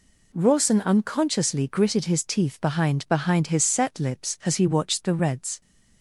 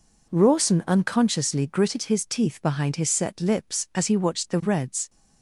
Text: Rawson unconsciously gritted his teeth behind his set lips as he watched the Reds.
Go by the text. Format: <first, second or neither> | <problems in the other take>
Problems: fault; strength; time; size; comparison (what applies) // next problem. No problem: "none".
second | says "behind" twice; at 3.0 s